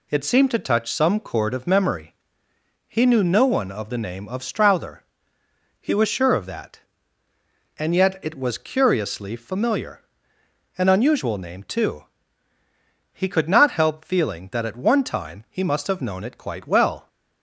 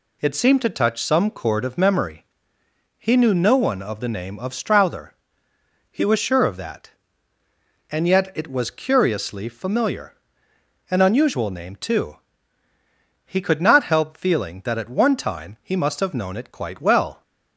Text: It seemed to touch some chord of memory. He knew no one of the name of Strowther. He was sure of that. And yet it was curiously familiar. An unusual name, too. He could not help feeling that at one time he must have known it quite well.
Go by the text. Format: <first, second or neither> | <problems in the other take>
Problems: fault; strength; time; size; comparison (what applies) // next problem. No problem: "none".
neither | none